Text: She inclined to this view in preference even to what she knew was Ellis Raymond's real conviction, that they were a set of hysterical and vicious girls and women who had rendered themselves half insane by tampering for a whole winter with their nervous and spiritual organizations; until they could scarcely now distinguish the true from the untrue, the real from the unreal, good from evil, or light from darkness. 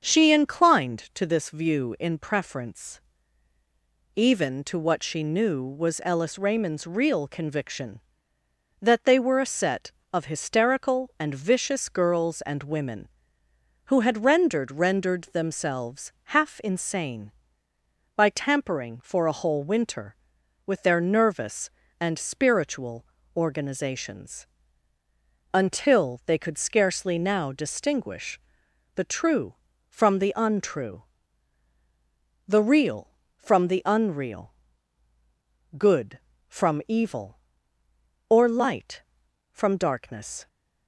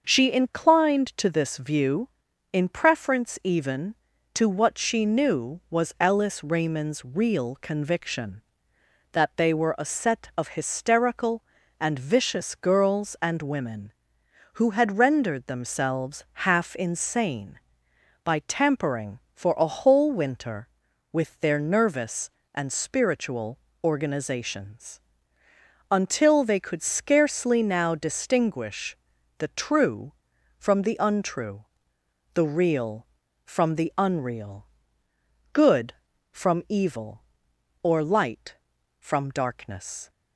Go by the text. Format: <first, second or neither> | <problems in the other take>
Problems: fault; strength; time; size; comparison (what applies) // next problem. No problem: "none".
second | starts louder than the rest; until 1.0 s; 7 dB; also in the second // pauses between "preference" and "even"; at 2.9 s; 1.1 s long // says "rendered" twice; at 14.7 s // pauses between "spiritual" and "organizations"; slight; at 23.0 s; 0.32 s long; slight in the second // pauses between "distinguish" and "the"; noticeable; at 28.3 s; 0.58 s long; also in the second